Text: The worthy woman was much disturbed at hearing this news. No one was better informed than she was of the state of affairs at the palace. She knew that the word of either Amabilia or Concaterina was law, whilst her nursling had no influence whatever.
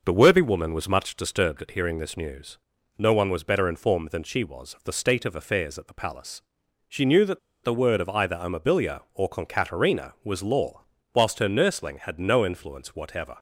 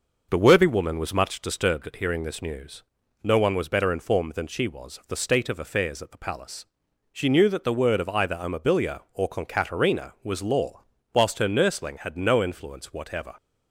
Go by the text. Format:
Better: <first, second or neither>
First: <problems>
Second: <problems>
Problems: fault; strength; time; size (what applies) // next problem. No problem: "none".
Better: second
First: pauses between "that" and "the"; slight; at 7.3 s; 0.25 s long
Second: none